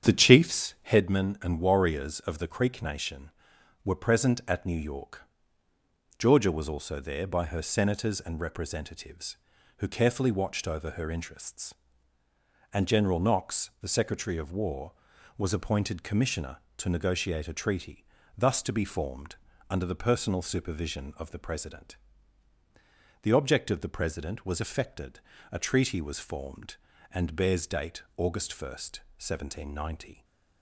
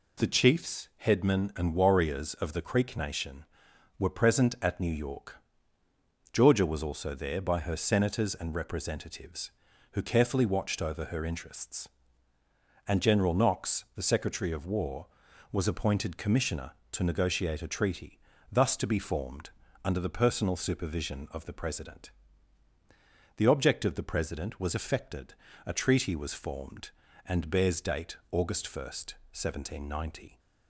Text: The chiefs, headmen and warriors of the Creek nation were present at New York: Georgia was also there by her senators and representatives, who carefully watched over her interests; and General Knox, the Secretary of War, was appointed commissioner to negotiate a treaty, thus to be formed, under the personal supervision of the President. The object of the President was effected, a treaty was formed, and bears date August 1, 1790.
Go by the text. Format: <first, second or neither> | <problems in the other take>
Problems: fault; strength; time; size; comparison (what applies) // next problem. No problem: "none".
second | starts louder than the rest; strong; until 1.1 s; 8.5 dB